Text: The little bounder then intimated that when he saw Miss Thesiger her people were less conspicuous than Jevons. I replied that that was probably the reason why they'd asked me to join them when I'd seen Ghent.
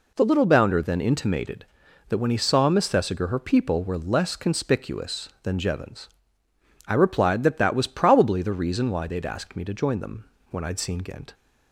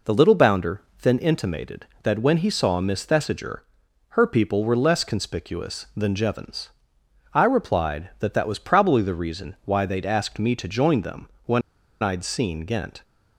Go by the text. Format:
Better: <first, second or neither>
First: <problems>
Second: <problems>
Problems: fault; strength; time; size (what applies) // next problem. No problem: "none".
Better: first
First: pauses between "them" and "when"; slight; at 10.2 s; 0.24 s long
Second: pauses between "bounder" and "then"; slight; at 0.8 s; 0.20 s long // pauses between "Thesiger" and "her"; noticeable; at 3.6 s; 0.50 s long // pauses between "them" and "when"; slight; at 11.2 s; 0.16 s long // pauses between "when" and "I'd"; at 11.6 s; 0.40 s long